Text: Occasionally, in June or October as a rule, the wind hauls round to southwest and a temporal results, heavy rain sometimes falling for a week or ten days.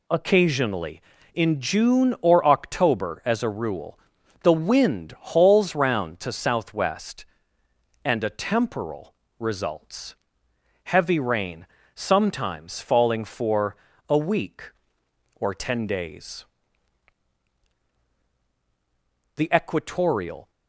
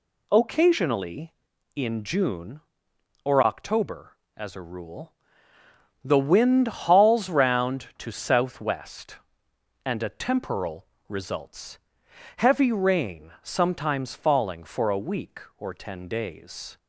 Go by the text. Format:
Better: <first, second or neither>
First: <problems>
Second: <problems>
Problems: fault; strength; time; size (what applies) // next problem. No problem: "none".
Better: second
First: pauses between "temporal" and "results"; slight; at 9.1 s; 0.26 s long // pauses between "rain" and "sometimes"; slight; at 11.6 s; 0.26 s long // pauses between "for" and "a"; slight; at 13.7 s; 0.32 s long // goes on to say "The equatorial"; noticeable; from 19.3 s on; 1.1 s long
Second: pauses between "temporal" and "results"; slight; at 10.8 s; 0.22 s long